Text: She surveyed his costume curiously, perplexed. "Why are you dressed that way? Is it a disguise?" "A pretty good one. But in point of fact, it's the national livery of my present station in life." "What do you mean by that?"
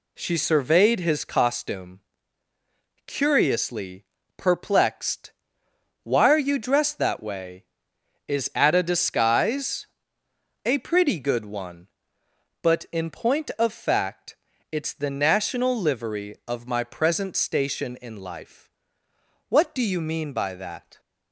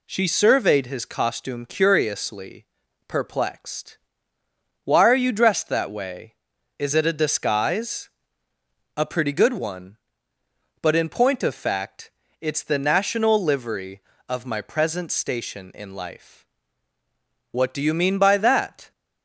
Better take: second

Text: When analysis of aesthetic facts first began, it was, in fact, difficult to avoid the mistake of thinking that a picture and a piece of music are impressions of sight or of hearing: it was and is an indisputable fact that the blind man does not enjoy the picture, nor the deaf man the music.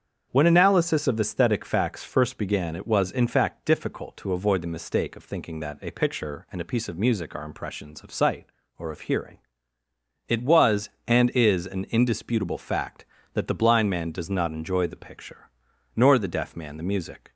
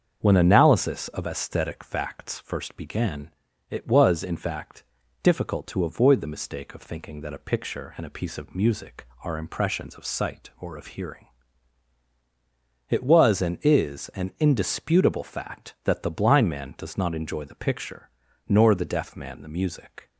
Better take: neither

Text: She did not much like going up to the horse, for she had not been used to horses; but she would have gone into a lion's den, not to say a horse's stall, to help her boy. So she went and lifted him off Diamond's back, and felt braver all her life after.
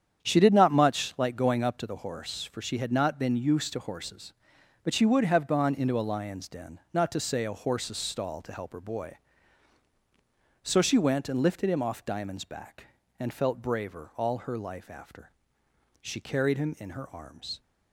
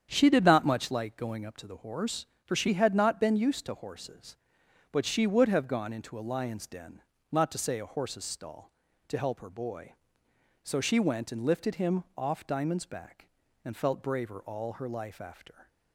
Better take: second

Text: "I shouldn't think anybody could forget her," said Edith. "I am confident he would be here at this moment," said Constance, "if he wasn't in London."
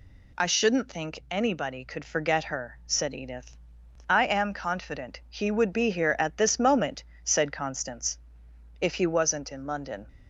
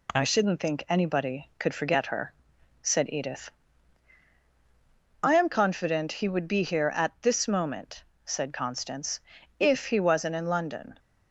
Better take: neither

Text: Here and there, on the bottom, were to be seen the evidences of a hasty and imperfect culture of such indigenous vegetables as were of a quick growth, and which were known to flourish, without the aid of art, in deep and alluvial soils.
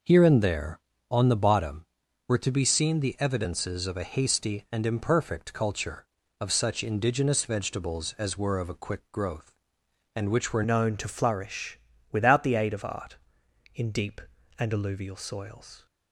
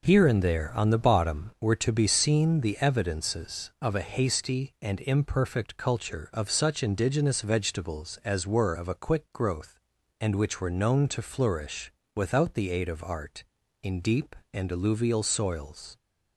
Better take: second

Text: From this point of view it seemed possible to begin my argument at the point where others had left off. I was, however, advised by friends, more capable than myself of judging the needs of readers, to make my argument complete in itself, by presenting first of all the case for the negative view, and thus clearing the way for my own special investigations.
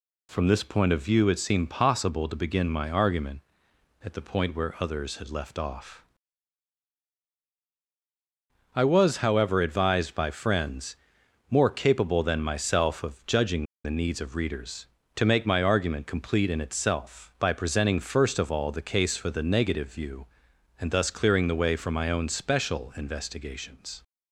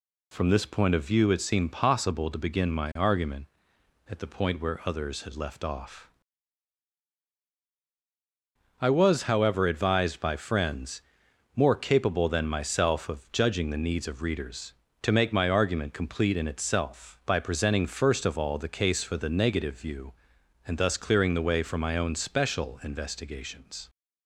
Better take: second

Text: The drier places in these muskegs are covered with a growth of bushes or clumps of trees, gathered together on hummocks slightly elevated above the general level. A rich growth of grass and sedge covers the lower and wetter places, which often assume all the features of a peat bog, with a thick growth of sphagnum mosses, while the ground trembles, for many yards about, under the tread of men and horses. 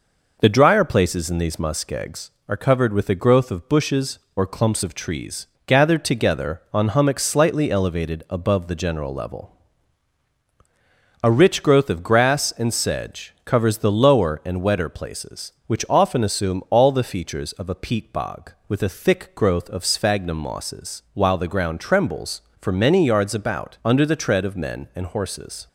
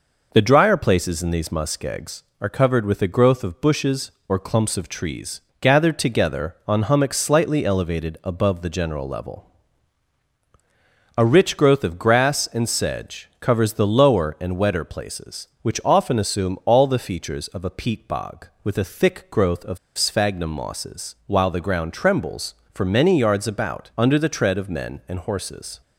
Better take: first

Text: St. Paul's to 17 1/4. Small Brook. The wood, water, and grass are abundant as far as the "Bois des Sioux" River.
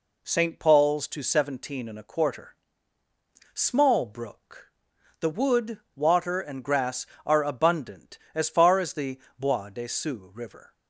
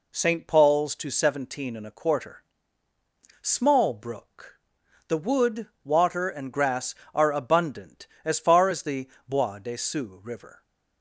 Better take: neither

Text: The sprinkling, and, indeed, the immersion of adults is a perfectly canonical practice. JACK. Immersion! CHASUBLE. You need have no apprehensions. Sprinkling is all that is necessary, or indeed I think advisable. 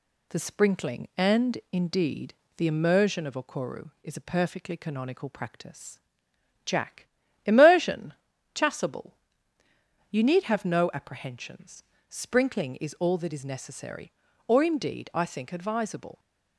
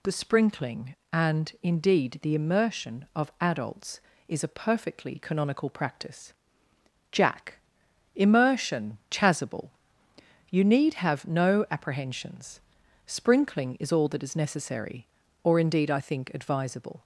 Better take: second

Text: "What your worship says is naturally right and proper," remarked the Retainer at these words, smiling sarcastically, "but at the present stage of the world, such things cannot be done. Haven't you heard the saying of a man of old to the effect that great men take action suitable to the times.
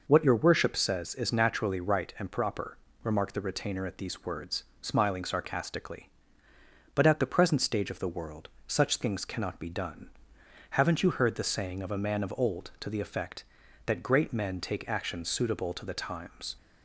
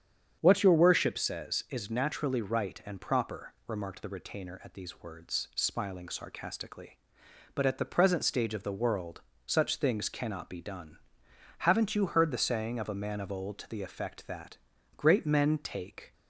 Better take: first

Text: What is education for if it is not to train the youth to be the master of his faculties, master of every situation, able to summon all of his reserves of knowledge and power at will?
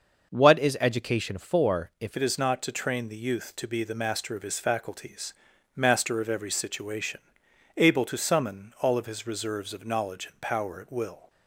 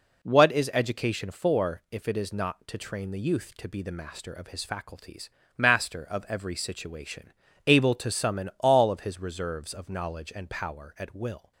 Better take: second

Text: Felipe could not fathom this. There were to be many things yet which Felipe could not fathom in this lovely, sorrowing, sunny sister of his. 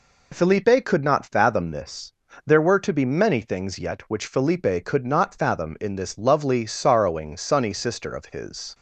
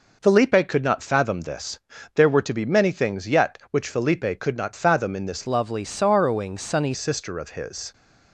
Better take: first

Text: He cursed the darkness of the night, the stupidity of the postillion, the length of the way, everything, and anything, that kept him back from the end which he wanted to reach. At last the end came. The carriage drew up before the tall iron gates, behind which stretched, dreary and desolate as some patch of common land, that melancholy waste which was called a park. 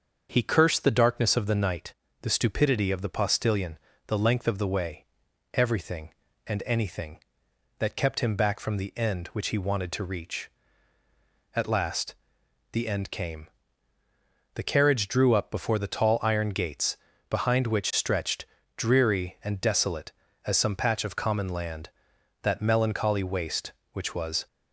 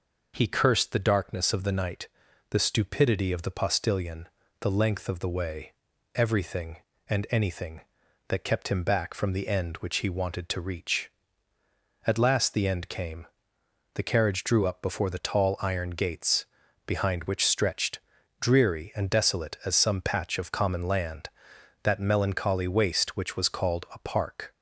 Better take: second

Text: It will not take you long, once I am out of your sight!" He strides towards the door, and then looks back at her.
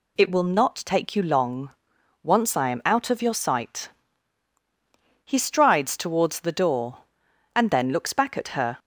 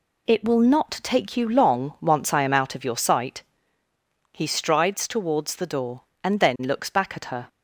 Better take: neither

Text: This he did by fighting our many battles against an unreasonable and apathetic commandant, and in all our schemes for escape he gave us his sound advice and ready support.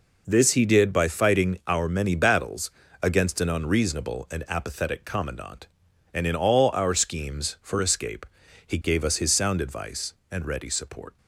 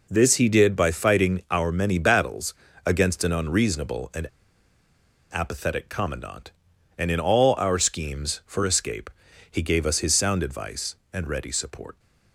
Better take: first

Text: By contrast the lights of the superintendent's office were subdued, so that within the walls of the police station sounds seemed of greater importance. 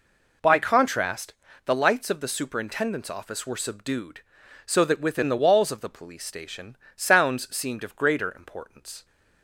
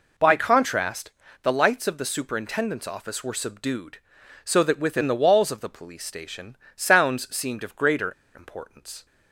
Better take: first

